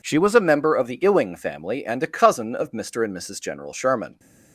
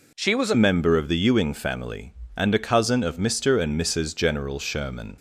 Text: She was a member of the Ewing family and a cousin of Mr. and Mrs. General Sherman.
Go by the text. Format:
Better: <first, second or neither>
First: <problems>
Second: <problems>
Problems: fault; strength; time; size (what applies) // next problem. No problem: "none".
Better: first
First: none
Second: changes voice at "member"; from 0.5 s on; 4.6 s long